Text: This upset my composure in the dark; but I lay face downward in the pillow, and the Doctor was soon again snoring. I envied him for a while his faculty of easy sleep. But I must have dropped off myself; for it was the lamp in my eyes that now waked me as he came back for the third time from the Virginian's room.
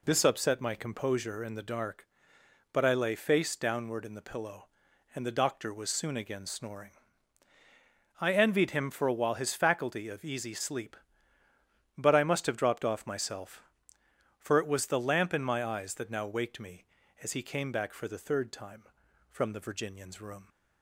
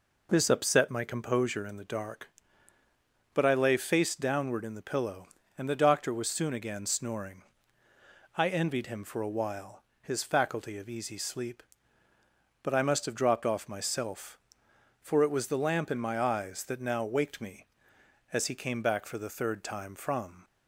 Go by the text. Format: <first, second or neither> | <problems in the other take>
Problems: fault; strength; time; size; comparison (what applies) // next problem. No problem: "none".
first | pauses between "while" and "his"; slight; at 9.8 s; 0.20 s long // stops before "the Virginian's room"; at 20.4 s